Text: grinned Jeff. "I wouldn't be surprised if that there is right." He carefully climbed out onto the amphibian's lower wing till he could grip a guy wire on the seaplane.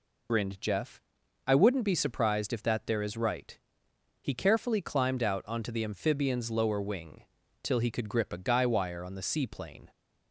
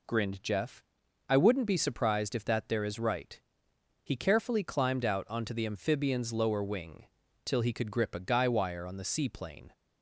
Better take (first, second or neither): second